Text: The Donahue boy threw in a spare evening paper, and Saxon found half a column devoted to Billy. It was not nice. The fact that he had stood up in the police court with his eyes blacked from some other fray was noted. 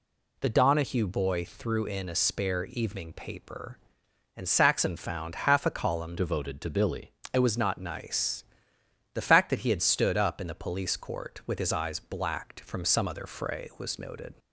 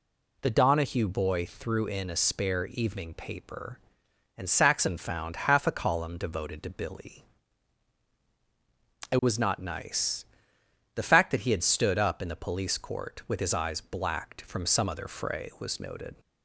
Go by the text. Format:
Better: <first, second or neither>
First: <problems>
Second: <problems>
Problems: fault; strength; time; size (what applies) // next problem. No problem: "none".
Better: second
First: changes voice from "devoted" to "Billy"; from 6.1 to 7.1 s; 1.0 s long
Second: none